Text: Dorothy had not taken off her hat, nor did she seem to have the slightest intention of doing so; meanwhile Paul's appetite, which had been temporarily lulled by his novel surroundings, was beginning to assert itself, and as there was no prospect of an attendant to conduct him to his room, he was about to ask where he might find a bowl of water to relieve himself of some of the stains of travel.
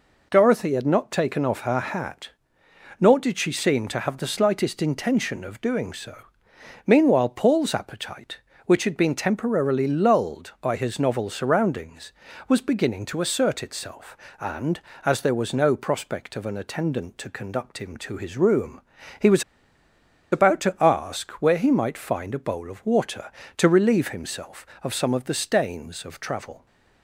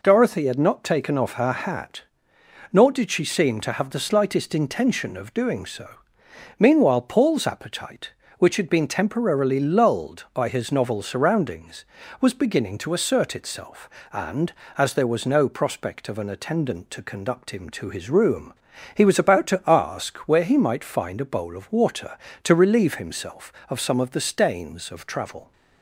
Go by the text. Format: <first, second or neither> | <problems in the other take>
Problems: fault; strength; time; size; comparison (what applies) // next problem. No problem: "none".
second | pauses between "was" and "about"; noticeable; at 19.4 s; 0.89 s long